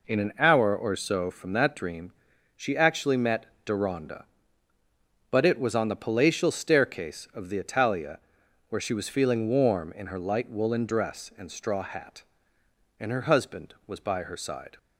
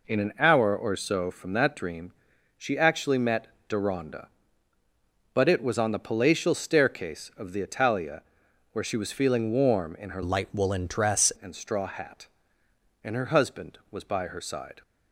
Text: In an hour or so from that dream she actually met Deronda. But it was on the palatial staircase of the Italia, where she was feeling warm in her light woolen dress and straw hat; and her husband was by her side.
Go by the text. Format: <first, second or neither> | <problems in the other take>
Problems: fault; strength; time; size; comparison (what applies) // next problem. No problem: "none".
first | pauses between "dream" and "she"; at 2.1 s; 0.44 s long; also in the first // pauses between "met" and "Deronda"; slight; at 3.4 s; 0.22 s long; slight in the first // changes voice from "light" to "dress"; from 10.2 to 11.3 s; 1.1 s long